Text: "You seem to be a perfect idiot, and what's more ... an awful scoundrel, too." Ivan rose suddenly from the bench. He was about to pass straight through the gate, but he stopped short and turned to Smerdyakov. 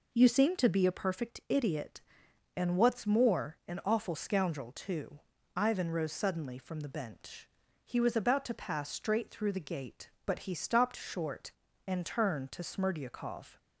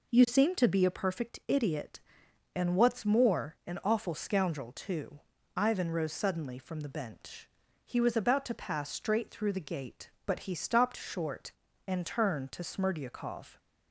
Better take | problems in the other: neither | none

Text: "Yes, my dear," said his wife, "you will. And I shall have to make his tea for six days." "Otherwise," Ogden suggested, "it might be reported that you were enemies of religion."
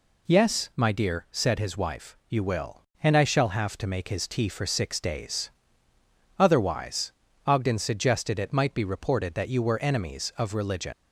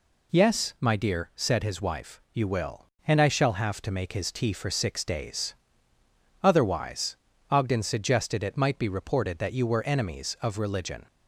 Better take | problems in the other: second | leaves "religion" unfinished; at 10.9 s; 95 ms

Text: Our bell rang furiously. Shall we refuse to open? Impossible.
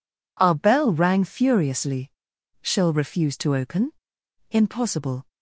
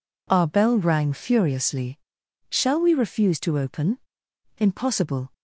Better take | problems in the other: second | skips "we"; at 2.9 s

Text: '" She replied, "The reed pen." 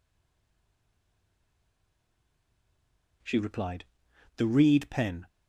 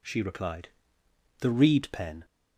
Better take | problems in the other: second | stays silent before the first word; strong; until 3.2 s; 3.2 s long

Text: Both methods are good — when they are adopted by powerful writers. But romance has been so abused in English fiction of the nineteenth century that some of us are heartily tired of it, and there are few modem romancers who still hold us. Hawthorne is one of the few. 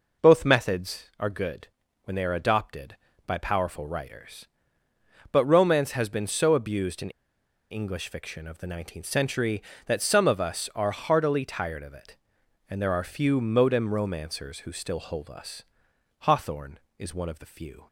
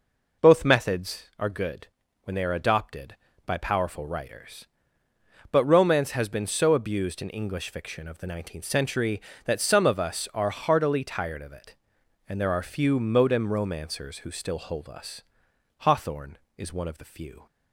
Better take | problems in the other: second | pauses between "in" and "English"; noticeable; at 7.1 s; 0.59 s long

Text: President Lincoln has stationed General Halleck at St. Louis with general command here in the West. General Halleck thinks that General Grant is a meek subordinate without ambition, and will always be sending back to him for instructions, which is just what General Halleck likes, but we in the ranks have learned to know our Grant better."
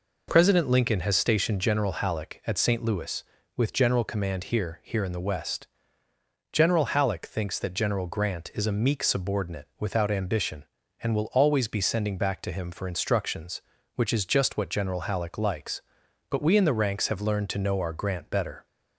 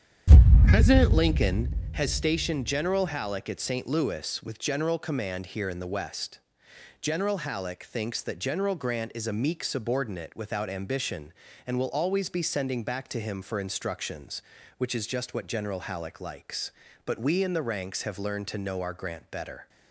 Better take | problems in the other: second | says "here" twice; at 4.8 s

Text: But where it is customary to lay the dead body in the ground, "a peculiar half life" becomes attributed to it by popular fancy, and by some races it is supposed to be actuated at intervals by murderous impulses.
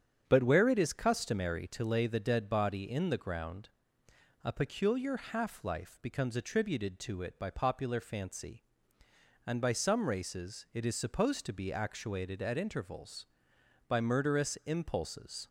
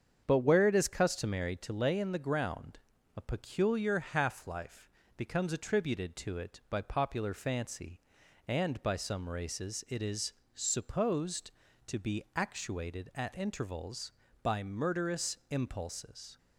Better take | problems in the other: first | starts louder than the rest; strong; until 1.2 s; 7.5 dB; strong in the first // skips "the dead body"; at 1.9 s // pauses between "life" and "becomes"; slight; at 4.8 s; 0.28 s long // pauses between "is" and "supposed"; slight; at 10.3 s; 0.24 s long

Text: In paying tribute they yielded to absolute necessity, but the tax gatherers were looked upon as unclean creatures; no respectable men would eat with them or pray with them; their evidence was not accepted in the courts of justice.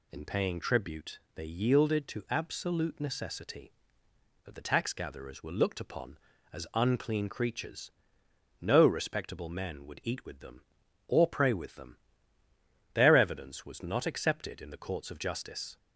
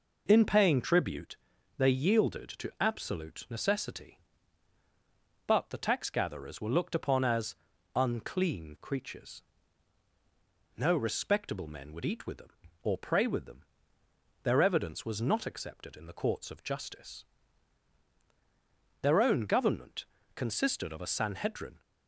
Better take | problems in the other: first | pauses between "tribute" and "they"; at 1.3 s; 0.40 s long; slight in the first // pauses between "as" and "unclean"; at 7.5 s; 0.40 s long // goes on to say "Their own government consisted of a Sanhedrin"; strong; from 19.0 s on; 2.7 s long

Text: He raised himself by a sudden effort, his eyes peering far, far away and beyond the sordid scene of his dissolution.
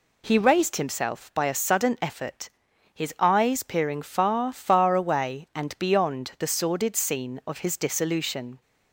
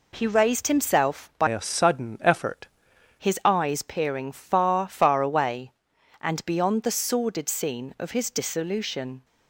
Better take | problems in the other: first | changes voice from "a" to "effort"; from 1.4 to 2.6 s; 1.2 s long

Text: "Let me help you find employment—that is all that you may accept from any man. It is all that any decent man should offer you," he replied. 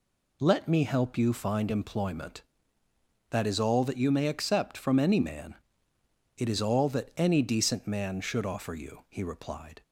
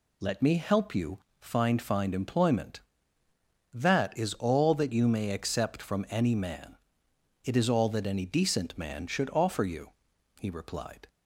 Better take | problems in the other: first | pauses between "you" and "find"; slight; at 1.1 s; 0.24 s long // says "find" twice; at 1.8 s

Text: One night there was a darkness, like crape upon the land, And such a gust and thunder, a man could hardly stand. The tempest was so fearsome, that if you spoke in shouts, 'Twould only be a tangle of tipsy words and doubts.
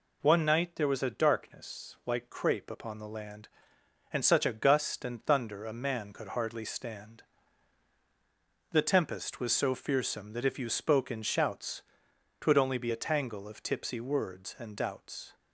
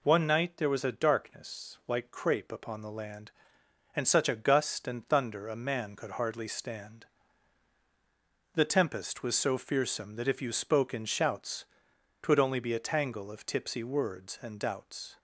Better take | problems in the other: neither | none

